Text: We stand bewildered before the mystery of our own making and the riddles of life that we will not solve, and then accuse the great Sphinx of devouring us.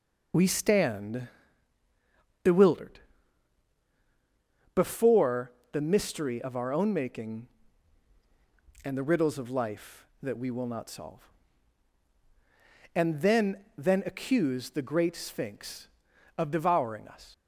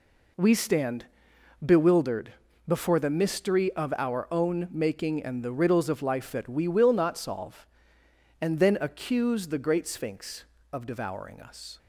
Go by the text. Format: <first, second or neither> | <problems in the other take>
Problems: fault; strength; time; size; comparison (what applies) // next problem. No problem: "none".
second | pauses between "stand" and "bewildered"; at 1.2 s; 1.1 s long; noticeable in the second // pauses between "bewildered" and "before"; strong; at 2.9 s; 1.7 s long; slight in the second // pauses between "before" and "the"; slight; at 5.5 s; 0.18 s long // says "then" twice; at 13.7 s